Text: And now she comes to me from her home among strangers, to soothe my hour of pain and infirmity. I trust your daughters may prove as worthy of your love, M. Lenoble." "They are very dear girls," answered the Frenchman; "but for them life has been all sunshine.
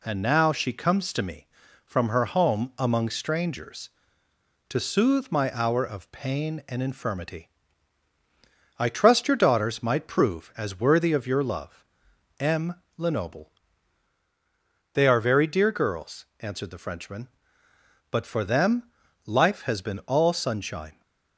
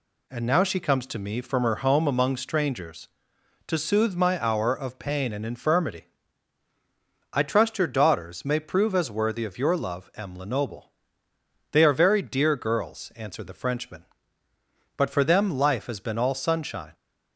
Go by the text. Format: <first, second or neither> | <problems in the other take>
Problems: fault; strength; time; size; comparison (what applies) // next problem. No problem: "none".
second | says "might" for "may"; at 9.8 s // pauses between "them" and "life"; at 18.8 s; 0.37 s long